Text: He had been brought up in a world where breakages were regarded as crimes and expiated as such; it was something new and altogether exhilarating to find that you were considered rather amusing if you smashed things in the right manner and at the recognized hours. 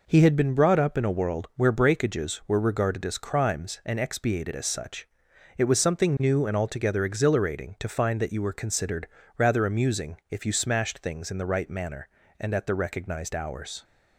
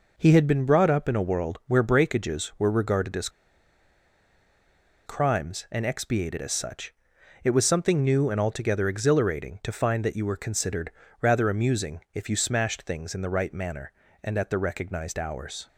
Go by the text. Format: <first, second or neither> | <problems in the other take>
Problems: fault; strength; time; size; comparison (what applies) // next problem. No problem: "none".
first | pauses between "as" and "crimes"; strong; at 3.2 s; 1.7 s long // pauses between "considered" and "rather"; slight; at 10.8 s; 0.30 s long; slight in the first